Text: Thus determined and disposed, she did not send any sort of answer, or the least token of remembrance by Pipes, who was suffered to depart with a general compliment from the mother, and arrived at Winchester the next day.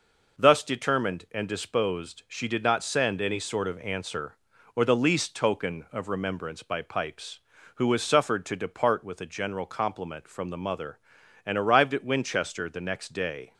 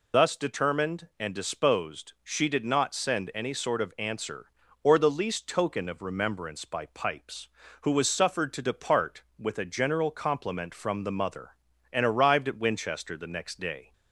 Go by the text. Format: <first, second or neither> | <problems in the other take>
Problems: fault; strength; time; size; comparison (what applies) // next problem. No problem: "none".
first | loses the start of "Thus"; at 0.1 s; 95 ms